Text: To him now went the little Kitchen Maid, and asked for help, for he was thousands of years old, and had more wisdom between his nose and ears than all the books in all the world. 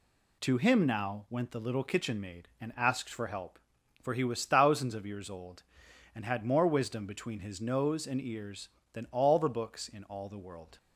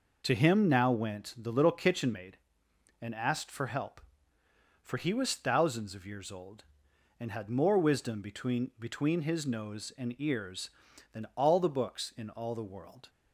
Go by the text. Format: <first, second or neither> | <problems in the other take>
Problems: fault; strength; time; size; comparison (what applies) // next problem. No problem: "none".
first | says "between" twice; at 8.7 s